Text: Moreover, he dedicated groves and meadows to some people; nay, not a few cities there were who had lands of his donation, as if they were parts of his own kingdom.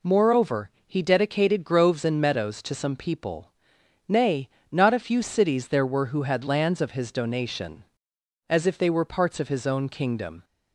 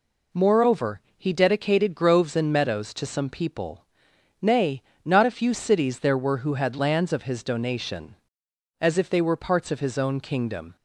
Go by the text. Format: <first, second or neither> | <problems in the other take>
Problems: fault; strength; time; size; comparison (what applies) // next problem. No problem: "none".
neither | none